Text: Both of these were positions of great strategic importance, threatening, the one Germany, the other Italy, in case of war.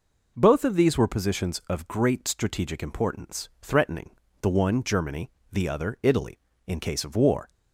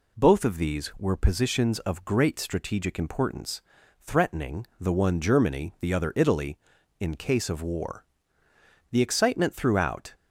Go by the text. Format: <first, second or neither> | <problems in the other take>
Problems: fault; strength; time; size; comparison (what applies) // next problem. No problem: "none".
first | goes on to say "The excitement throughout"; noticeable; from 8.9 s on; 1.2 s long